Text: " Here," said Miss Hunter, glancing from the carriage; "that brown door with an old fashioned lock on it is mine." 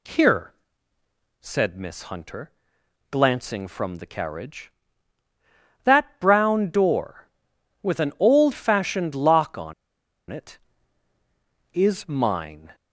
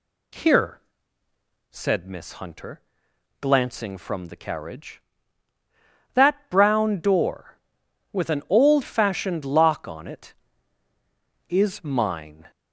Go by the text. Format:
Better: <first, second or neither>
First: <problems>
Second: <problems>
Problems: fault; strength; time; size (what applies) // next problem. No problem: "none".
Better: second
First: pauses between "on" and "it"; noticeable; at 9.7 s; 0.57 s long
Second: none